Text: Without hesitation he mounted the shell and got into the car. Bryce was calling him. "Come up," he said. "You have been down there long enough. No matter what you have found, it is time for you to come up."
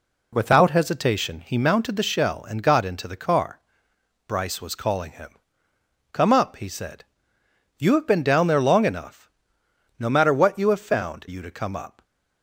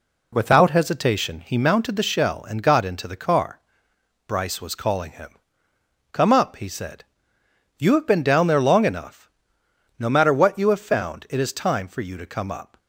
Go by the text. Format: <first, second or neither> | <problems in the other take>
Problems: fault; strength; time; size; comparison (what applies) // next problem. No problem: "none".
second | skips "it is time for"; at 11.2 s